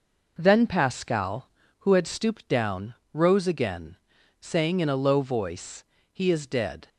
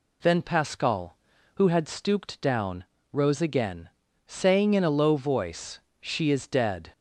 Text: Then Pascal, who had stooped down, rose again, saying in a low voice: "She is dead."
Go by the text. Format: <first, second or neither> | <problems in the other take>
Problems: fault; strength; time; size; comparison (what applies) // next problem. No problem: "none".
second | says "He" for "She"; at 6.1 s